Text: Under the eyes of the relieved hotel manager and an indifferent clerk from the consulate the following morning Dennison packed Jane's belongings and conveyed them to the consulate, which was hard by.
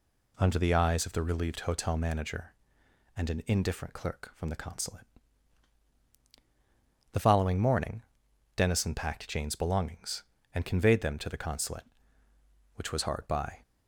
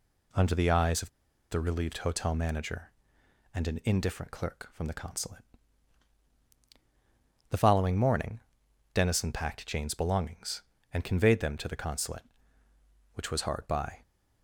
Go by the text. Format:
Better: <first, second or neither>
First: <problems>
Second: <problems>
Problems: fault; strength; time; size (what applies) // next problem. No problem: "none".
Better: first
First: pauses between "consulate" and "the"; strong; at 5.0 s; 2.0 s long // pauses between "morning" and "Dennison"; noticeable; at 8.0 s; 0.54 s long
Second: pauses between "of" and "the"; at 1.0 s; 0.42 s long // pauses between "consulate" and "the"; strong; at 5.4 s; 2.0 s long // pauses between "morning" and "Dennison"; noticeable; at 8.3 s; 0.54 s long